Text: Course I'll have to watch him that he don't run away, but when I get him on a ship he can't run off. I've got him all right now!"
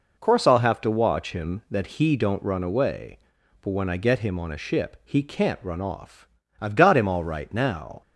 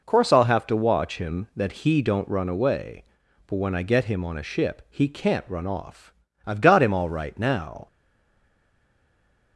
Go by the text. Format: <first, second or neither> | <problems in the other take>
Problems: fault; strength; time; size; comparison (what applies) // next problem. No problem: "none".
first | stays silent after the last word; noticeable; from 7.8 s on; 1.7 s long